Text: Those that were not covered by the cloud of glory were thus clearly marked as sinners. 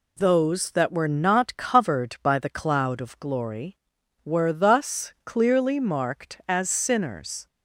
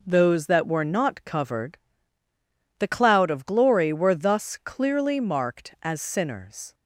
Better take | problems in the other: first | skips "by"; at 2.2 s

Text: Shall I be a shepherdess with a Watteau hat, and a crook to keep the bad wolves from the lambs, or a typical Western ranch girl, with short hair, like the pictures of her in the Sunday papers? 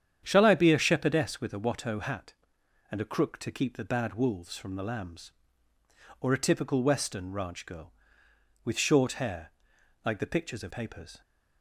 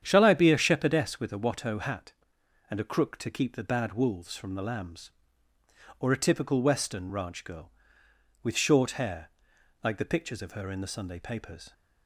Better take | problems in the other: second | starts louder than the rest; strong; until 1.2 s; 9 dB; strong in the second // skips "her in the Sunday"; at 10.7 s

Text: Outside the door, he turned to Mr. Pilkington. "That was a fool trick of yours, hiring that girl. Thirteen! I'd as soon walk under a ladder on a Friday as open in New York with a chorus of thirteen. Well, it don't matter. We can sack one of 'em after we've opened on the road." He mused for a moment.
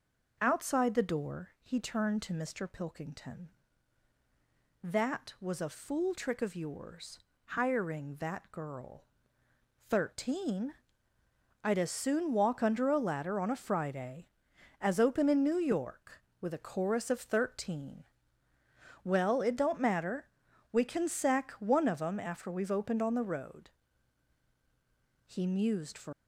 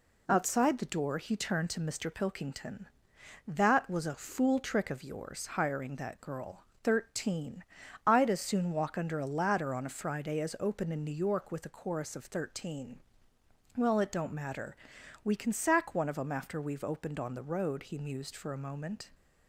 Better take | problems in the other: second | stops before "a moment"; at 26.1 s

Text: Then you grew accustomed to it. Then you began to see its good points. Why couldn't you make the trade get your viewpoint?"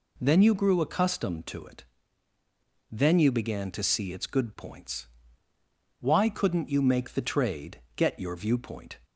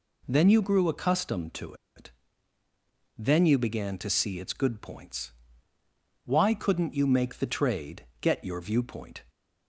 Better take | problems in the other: first | pauses between "to" and "it"; slight; at 1.7 s; 0.23 s long // pauses between "trade" and "get"; slight; at 8.0 s; 0.16 s long; slight in the first

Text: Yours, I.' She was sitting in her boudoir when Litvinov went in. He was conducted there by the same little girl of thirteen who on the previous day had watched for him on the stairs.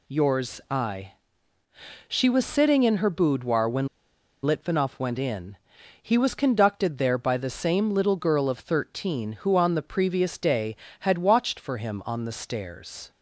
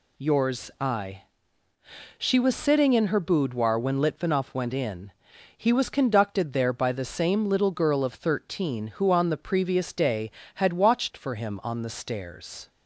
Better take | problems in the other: second | pauses between "when" and "Litvinov"; noticeable; at 3.8 s; 0.56 s long

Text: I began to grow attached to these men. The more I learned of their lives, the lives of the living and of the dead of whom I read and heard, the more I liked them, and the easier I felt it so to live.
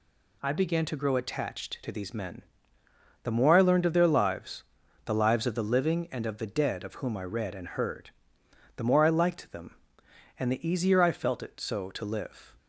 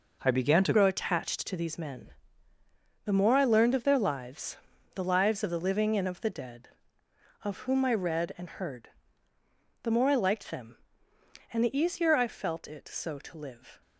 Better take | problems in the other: first | changes voice at "grow"; from 0.7 s on; 13.1 s long

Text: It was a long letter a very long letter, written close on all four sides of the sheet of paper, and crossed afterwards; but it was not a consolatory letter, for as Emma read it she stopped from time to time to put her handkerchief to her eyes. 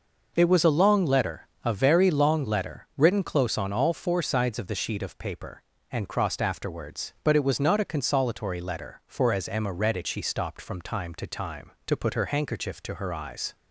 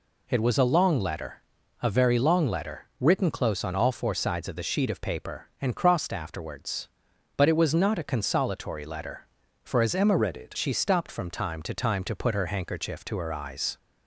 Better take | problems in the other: first | pauses between "letter" and "a"; at 1.4 s; 0.42 s long; slight in the first // changes voice from "read" to "it"; from 10.1 to 10.5 s; 0.4 s long

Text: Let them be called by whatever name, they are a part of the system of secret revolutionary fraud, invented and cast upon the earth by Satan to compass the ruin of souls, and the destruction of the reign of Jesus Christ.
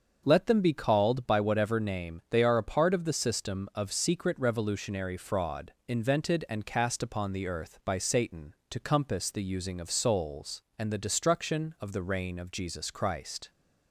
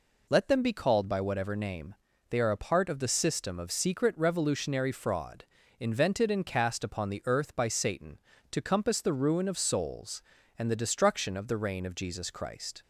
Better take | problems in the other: second | starts louder than the rest; until 1.2 s; 7 dB // says "using" for "ruin"; at 9.4 s

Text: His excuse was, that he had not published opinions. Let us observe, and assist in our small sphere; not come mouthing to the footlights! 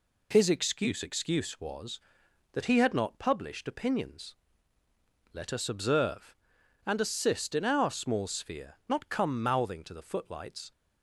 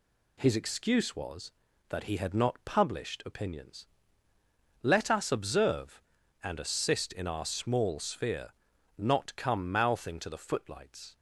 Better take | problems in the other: second | says "excuse" twice; at 1.0 s

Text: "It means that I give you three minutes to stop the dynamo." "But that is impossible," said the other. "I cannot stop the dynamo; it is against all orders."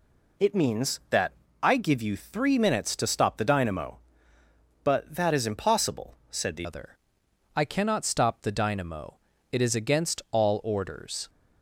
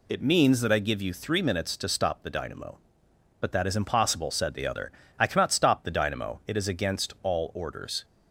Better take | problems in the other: second | pauses between "that" and "I"; slight; at 1.3 s; 0.30 s long // changes voice at "other"; from 6.6 s on; 4.6 s long

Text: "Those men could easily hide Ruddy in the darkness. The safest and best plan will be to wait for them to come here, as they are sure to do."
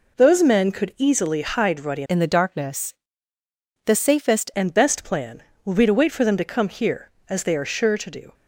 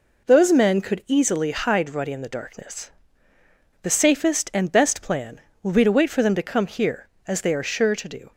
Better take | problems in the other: second | changes voice from "in" to "safest"; from 2.0 to 4.4 s; 2.4 s long

